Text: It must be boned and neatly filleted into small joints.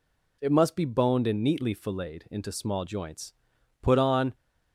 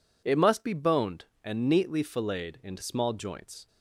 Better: second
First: goes on to say "Put on"; from 3.8 s on; 0.52 s long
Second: none

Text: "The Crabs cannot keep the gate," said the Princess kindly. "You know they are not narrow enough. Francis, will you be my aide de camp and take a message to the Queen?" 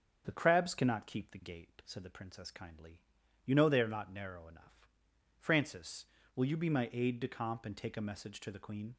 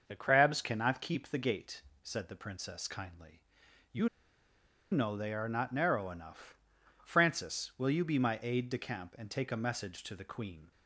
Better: first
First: starts louder than the rest; strong; until 1.2 s; 7.5 dB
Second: starts louder than the rest; until 1.0 s; 6.5 dB // pauses between "You" and "know"; noticeable; at 4.0 s; 0.84 s long

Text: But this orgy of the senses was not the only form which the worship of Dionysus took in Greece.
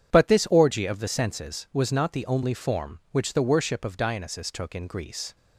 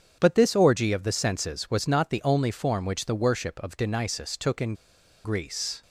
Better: first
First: starts louder than the rest; strong; until 1.1 s; 8.5 dB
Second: starts louder than the rest; strong; until 1.2 s; 7.5 dB // pauses between "in" and "Greece"; noticeable; at 4.7 s; 0.49 s long

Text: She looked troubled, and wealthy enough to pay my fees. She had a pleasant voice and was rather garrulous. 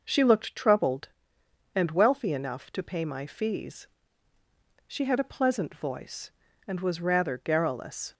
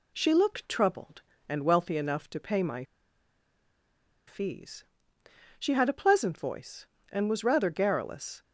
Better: first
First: none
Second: pauses between "my" and "fees"; strong; at 2.8 s; 1.4 s long

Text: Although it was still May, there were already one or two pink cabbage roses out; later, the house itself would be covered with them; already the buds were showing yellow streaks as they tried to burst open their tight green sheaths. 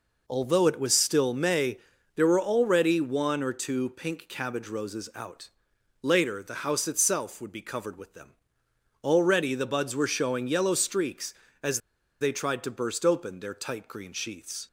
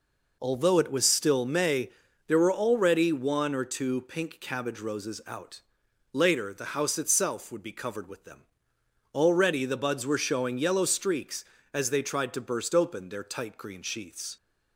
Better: second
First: pauses between "as" and "they"; at 11.7 s; 0.42 s long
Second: none

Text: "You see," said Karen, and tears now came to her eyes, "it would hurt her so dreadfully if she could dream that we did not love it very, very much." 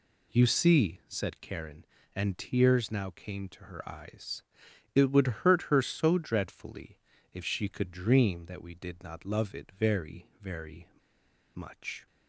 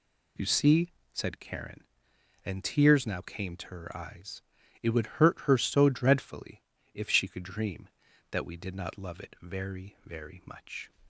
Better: second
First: pauses between "dreadfully" and "if"; slight; at 6.9 s; 0.34 s long // pauses between "very" and "much"; noticeable; at 10.8 s; 0.67 s long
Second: pauses between "dreadfully" and "if"; slight; at 6.6 s; 0.32 s long

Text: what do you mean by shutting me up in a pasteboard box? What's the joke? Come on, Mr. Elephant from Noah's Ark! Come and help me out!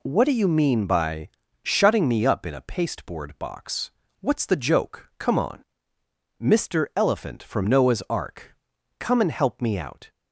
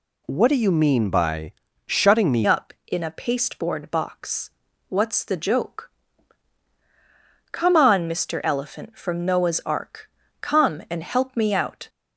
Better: first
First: pauses between "by" and "shutting"; slight; at 1.2 s; 0.34 s long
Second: pauses between "by" and "shutting"; slight; at 1.5 s; 0.34 s long // changes voice at "up"; from 2.4 s on; 9.4 s long

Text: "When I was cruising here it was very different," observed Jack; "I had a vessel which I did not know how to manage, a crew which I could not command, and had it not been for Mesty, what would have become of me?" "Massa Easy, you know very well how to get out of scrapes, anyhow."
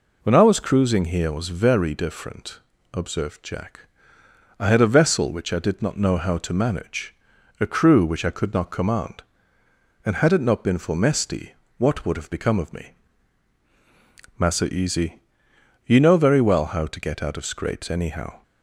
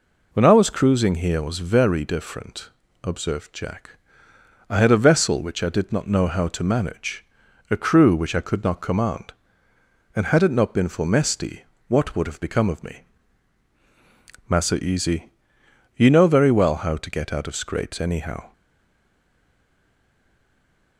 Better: first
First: none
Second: stays silent after the last word; from 18.5 s on; 2.4 s long

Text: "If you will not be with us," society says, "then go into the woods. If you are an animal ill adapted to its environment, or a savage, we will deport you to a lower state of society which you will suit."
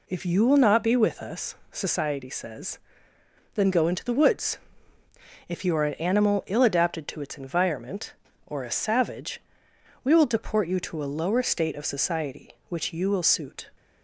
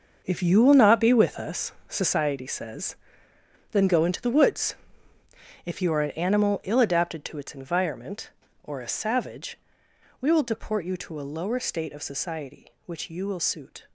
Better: first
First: none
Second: gets quieter; strong; throughout; 11 dB

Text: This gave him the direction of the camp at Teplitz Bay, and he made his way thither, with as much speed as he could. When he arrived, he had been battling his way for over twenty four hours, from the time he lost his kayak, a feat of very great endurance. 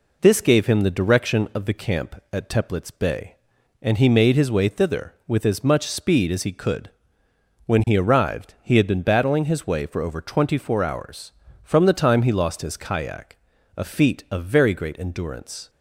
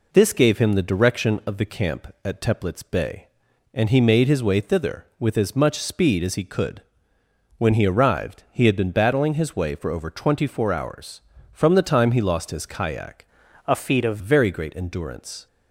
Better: first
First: none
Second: changes voice from "a" to "of"; from 13.6 to 14.1 s; 0.5 s long

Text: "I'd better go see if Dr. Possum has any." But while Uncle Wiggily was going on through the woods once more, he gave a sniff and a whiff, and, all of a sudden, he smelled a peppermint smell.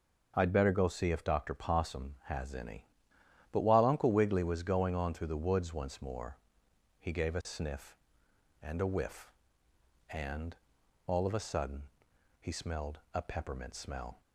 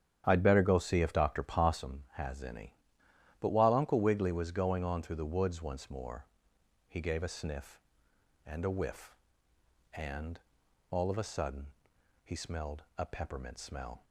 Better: first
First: none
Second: starts louder than the rest; strong; until 1.9 s; 9.5 dB

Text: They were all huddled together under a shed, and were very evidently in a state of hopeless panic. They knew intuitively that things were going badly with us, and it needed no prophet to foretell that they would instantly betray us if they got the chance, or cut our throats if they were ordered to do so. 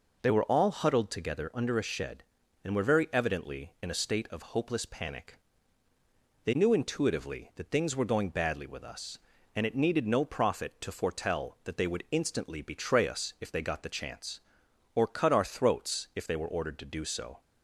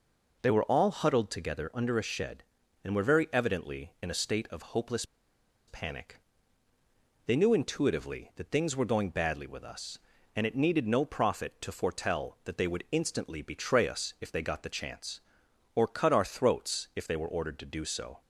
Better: first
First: none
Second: pauses between "hopeless" and "panic"; noticeable; at 5.0 s; 0.64 s long

